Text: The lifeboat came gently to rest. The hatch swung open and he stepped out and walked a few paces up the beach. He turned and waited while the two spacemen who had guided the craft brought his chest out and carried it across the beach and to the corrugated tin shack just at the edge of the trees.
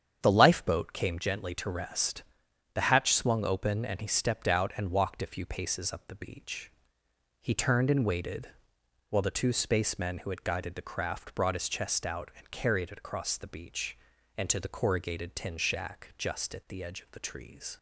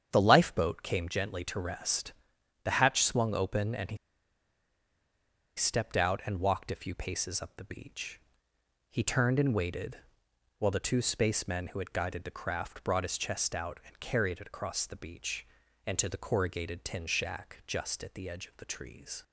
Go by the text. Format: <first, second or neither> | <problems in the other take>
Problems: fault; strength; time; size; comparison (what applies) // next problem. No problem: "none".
first | starts louder than the rest; strong; until 1.1 s; 8 dB; strong in the first // pauses between "he" and "stepped"; strong; at 3.9 s; 1.6 s long // pauses between "waited" and "while"; noticeable; at 9.9 s; 0.62 s long; noticeable in the first